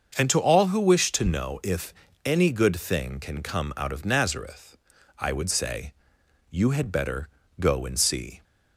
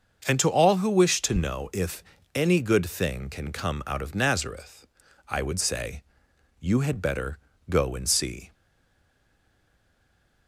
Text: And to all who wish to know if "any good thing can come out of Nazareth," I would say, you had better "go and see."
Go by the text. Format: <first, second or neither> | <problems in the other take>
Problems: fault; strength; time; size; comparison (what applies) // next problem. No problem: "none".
first | starts louder than the rest; until 1.2 s; 6.5 dB; also in the first // pauses between "if" and "any"; slight; at 2.0 s; 0.32 s long; slight in the first // pauses between "better" and "go"; slight; at 7.3 s; 0.30 s long; slight in the first // stays silent after the last word; noticeable; from 8.5 s on; 1.9 s long